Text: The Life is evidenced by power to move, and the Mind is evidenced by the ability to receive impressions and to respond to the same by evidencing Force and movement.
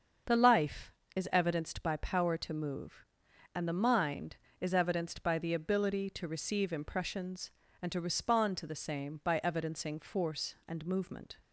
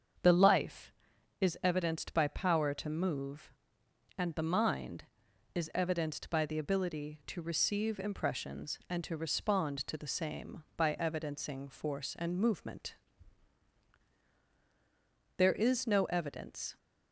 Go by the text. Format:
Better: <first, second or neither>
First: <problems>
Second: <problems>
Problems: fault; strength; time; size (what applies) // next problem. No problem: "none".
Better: first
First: starts louder than the rest; until 1.5 s; 7 dB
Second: starts louder than the rest; strong; until 1.7 s; 7 dB // goes on to say "There is no evidence"; from 15.3 s on; 1.4 s long